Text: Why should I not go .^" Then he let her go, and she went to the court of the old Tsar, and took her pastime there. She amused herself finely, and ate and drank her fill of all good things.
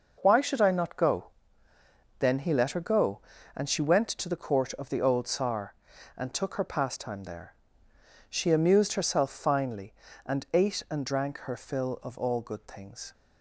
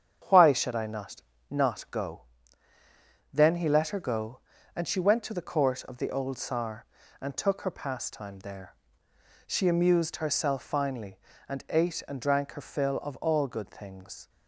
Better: first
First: none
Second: starts louder than the rest; strong; until 1.5 s; 8 dB // says "not" twice; at 1.5 s

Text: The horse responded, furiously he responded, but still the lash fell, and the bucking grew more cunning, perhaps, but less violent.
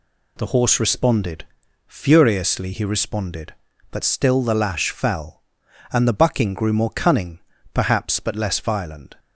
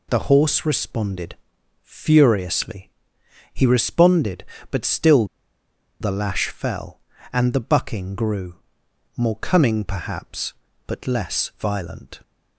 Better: first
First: none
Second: pauses between "furiously" and "he"; noticeable; at 2.8 s; 0.62 s long // pauses between "still" and "the"; noticeable; at 5.2 s; 0.74 s long // pauses between "grew" and "more"; noticeable; at 8.5 s; 0.62 s long

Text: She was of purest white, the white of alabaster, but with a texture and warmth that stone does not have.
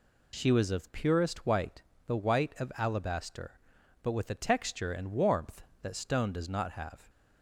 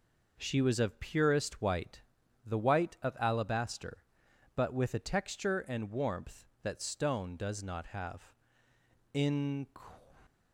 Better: first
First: none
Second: goes on to say "In"; from 9.1 s on; 0.54 s long

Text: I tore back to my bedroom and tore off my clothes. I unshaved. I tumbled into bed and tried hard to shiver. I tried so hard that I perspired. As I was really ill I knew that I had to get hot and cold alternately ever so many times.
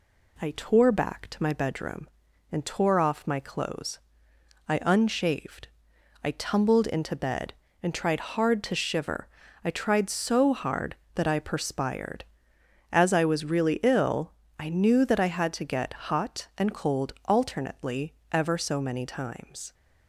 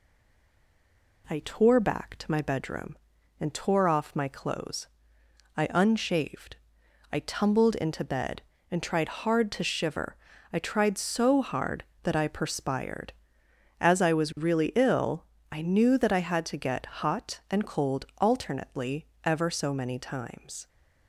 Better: first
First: pauses between "ill" and "I"; slight; at 14.3 s; 0.26 s long // pauses between "alternately" and "ever"; slight; at 18.1 s; 0.16 s long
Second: stays silent before the first word; noticeable; until 1.2 s; 1.2 s long // pauses between "ill" and "I"; slight; at 15.2 s; 0.26 s long // pauses between "alternately" and "ever"; slight; at 19.0 s; 0.16 s long

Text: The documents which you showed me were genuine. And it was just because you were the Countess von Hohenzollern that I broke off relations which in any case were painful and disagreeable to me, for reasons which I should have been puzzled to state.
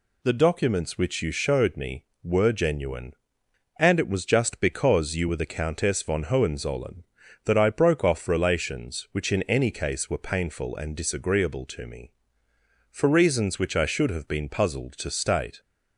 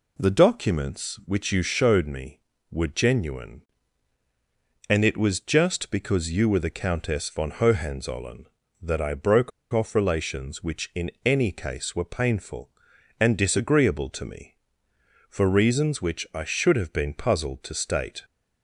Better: first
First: none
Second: pauses between "broke" and "off"; slight; at 9.5 s; 0.22 s long

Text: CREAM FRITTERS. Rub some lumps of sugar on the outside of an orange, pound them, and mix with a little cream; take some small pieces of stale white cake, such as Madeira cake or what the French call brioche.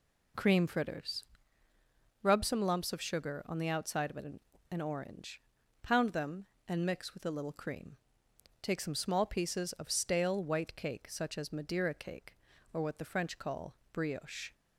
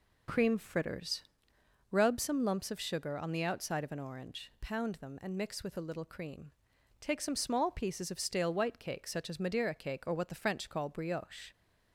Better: second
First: says "an" twice; at 4.7 s // pauses between "call" and "brioche"; slight; at 13.7 s; 0.16 s long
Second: none

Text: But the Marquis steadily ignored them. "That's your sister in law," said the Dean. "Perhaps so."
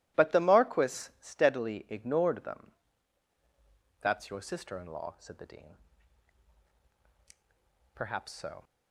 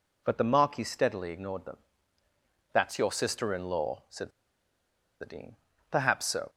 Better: first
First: none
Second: pauses between "said" and "the"; noticeable; at 4.3 s; 0.90 s long

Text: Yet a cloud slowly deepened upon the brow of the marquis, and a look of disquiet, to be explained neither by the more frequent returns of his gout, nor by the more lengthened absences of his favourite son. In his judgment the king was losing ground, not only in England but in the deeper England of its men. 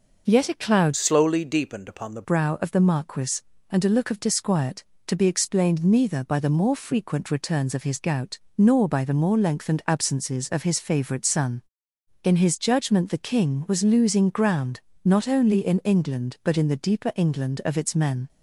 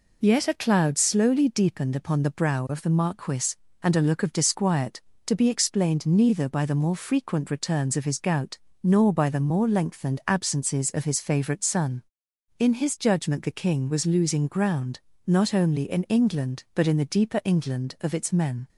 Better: second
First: changes voice from "slowly" to "the"; from 0.9 to 2.2 s; 1.3 s long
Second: none

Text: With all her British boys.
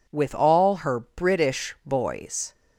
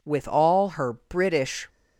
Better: first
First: none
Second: stops before "boys"; at 1.6 s

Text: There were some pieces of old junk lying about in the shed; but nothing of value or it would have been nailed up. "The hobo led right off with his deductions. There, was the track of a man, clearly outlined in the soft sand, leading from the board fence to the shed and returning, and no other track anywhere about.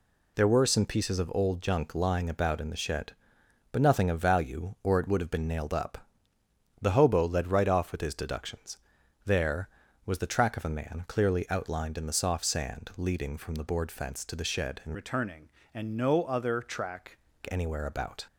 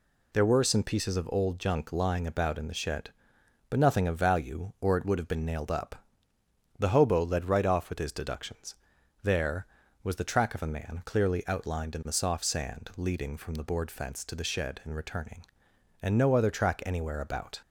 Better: second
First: changes voice from "returning" to "track"; from 14.9 to 17.1 s; 2.2 s long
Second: none

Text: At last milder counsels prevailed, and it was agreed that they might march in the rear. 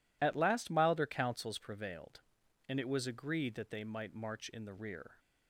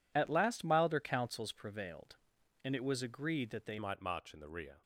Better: first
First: none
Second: changes voice at "might"; from 3.7 s on; 1.1 s long

